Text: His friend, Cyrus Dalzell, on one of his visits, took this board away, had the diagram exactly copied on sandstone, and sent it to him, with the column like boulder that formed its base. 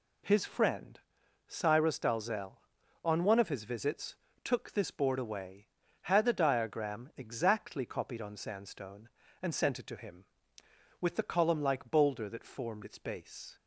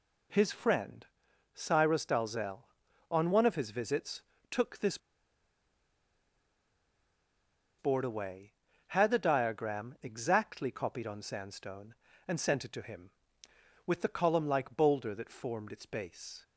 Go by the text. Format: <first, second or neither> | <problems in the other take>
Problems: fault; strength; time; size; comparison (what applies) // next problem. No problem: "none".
first | pauses between "this" and "board"; strong; at 4.9 s; 2.8 s long